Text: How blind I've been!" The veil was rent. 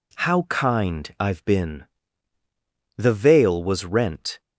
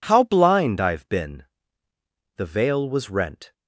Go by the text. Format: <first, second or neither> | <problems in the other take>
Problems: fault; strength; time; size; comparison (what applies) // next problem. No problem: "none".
second | says "kind" for "blind"; at 0.4 s